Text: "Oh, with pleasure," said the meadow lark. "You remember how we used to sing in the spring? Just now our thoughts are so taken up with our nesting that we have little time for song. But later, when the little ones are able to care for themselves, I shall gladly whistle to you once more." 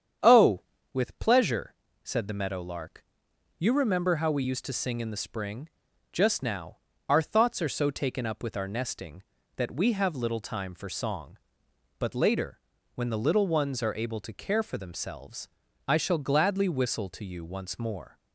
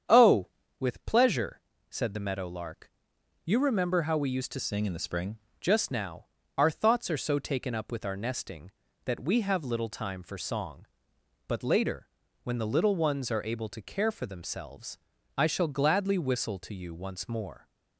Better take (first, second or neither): first